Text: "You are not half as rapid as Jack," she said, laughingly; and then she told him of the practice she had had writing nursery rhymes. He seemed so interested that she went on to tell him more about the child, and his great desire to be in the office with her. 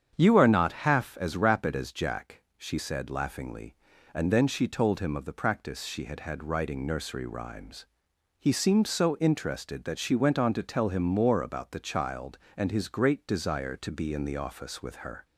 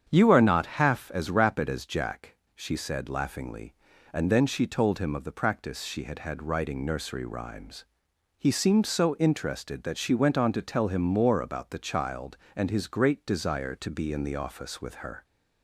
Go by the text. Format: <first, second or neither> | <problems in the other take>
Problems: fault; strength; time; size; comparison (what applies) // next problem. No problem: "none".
neither | starts louder than the rest; strong; the same in both